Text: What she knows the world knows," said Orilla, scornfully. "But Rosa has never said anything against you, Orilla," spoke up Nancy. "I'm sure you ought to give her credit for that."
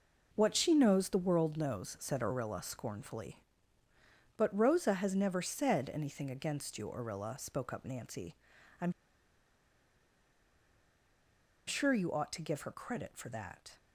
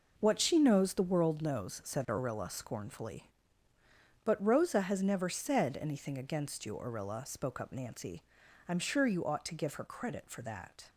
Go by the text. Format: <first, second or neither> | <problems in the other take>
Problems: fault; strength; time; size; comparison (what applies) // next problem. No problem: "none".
second | pauses between "I'm" and "sure"; strong; at 8.9 s; 2.7 s long